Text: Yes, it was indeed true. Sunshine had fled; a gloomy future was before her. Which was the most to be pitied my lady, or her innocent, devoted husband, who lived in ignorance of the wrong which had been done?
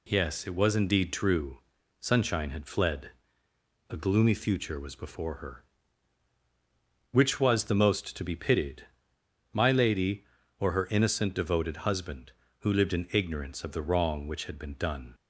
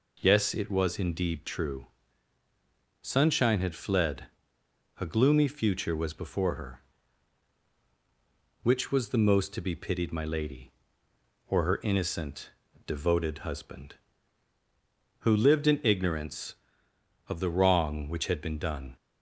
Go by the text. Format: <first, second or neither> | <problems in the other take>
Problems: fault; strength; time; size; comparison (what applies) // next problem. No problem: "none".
second | pauses between "pitied" and "my"; noticeable; at 8.8 s; 0.68 s long